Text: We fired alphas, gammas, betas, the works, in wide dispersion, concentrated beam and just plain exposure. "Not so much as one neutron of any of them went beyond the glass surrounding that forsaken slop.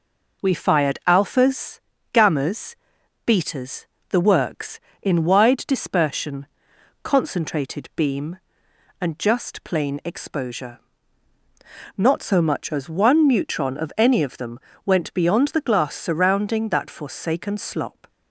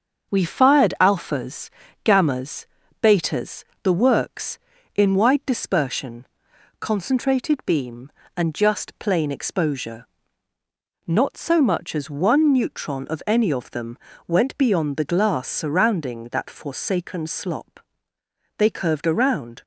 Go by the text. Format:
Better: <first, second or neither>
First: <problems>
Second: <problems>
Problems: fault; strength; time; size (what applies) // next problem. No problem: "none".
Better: first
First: pauses between "them" and "went"; slight; at 14.5 s; 0.24 s long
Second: starts louder than the rest; until 1.3 s; 7 dB // pauses between "them" and "went"; slight; at 13.9 s; 0.30 s long // goes on to say "They curved around"; noticeable; from 18.5 s on; 1.0 s long